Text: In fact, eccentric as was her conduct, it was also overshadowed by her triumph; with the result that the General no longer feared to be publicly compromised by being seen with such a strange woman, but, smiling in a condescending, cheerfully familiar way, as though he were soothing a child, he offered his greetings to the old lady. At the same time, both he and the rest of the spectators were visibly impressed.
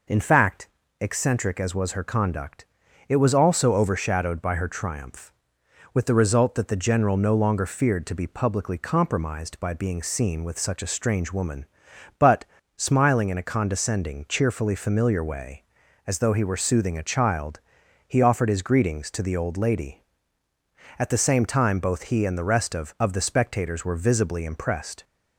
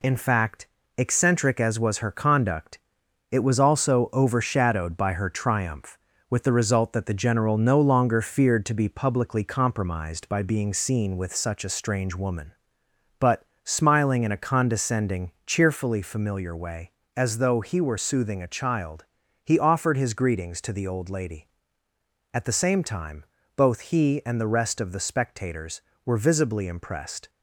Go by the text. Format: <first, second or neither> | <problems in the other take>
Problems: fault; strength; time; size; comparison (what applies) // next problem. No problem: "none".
second | says "of" twice; at 22.9 s